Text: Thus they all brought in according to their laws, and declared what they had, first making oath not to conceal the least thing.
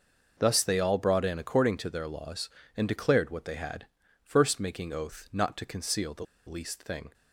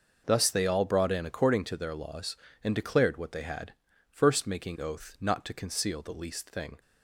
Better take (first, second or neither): second